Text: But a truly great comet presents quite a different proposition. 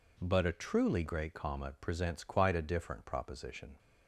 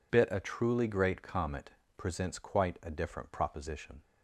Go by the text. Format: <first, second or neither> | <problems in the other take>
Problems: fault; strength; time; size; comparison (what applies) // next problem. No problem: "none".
first | says "Bit" for "But"; at 0.1 s // pauses between "comet" and "presents"; slight; at 1.6 s; 0.26 s long